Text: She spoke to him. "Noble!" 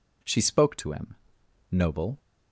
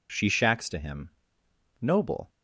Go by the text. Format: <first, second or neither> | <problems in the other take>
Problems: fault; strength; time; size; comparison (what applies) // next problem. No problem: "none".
first | says "shacks" for "spoke"; at 0.2 s